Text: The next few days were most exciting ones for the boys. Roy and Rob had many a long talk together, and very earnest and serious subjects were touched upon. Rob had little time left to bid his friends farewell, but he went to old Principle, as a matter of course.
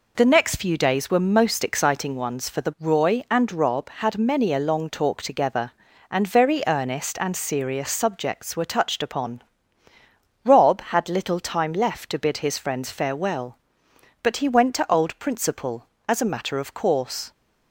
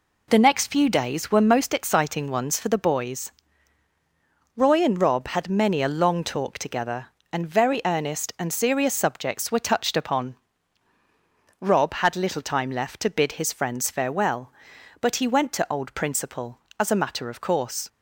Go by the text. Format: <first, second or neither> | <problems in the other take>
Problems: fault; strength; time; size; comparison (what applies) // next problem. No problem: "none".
second | skips "boys"; at 2.7 s